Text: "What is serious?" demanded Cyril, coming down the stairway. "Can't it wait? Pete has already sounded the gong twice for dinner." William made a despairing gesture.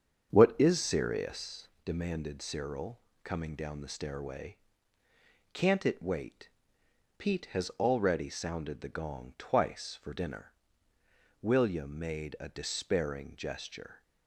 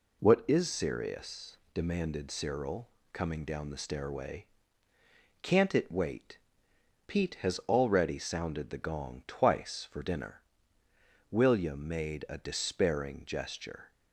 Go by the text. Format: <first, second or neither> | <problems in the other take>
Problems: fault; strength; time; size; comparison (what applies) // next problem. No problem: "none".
second | starts louder than the rest; strong; until 1.8 s; 7 dB